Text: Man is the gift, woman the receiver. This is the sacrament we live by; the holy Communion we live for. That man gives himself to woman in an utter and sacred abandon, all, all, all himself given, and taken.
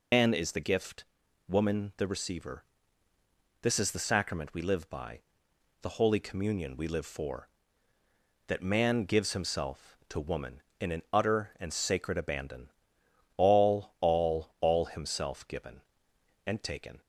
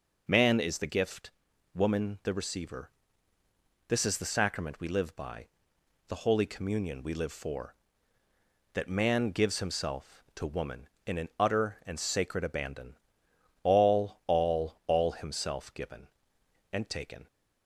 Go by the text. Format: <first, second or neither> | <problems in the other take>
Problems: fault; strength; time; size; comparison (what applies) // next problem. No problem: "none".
second | loses the start of "Man"; at 0.1 s; 100 ms